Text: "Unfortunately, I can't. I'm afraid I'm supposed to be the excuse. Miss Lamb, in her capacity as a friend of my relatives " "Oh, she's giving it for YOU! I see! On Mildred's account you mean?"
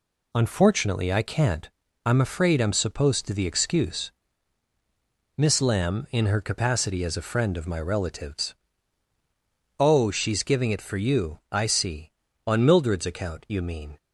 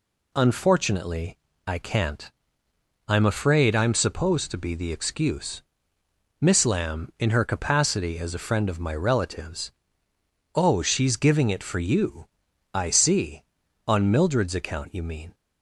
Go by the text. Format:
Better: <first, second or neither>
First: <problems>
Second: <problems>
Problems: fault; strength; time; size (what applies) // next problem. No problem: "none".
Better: second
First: skips "be"; at 3.3 s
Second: none